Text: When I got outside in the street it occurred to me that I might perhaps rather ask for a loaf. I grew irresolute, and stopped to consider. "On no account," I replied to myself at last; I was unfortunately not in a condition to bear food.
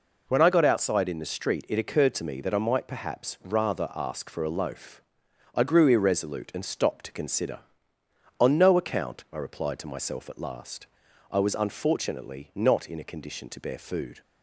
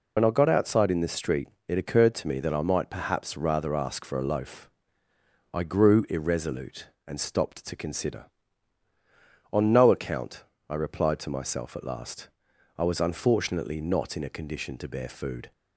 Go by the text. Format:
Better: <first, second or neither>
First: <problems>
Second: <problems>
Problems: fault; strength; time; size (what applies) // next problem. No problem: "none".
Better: first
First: none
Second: loses the start of "When"; at 0.1 s; 70 ms // pauses between "street" and "it"; slight; at 1.4 s; 0.20 s long